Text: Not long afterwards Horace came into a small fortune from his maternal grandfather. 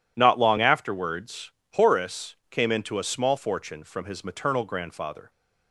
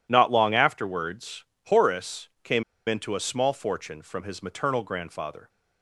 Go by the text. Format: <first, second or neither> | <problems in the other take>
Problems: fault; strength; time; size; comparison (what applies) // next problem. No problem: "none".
first | pauses between "afterwards" and "Horace"; slight; at 1.4 s; 0.22 s long; slight in the first // pauses between "came" and "into"; slight; at 2.6 s; 0.25 s long